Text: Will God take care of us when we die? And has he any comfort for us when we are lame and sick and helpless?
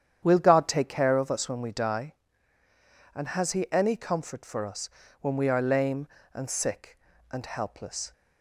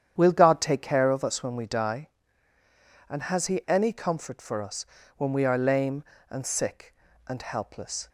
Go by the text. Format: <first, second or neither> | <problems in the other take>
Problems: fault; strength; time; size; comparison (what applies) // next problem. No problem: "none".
neither | starts louder than the rest; strong; the same in both // pauses between "us" and "when"; slight; the same in both